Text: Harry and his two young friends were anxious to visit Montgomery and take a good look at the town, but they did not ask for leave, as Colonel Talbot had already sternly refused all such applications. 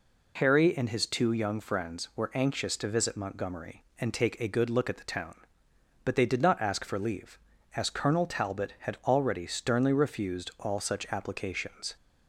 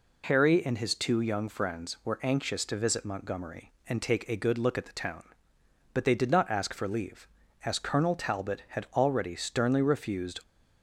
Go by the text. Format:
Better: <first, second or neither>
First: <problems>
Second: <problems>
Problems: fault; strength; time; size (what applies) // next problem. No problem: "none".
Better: first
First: none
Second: stops before "all such applications"; at 10.4 s